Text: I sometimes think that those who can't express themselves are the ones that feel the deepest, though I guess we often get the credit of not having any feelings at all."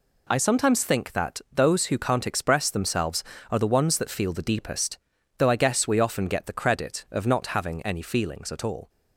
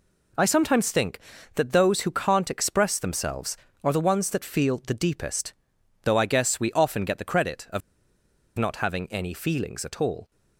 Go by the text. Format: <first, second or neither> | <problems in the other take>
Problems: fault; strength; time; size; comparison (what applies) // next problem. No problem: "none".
first | pauses between "of" and "not"; noticeable; at 7.8 s; 0.77 s long